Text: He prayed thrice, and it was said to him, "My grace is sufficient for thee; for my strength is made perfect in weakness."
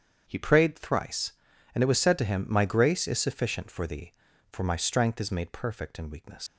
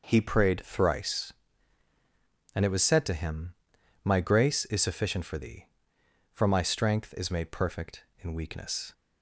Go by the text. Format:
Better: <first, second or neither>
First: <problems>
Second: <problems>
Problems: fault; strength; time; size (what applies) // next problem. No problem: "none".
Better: second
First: starts louder than the rest; strong; until 1.2 s; 7.5 dB // leaves "weakness" unfinished; at 6.4 s; 110 ms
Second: none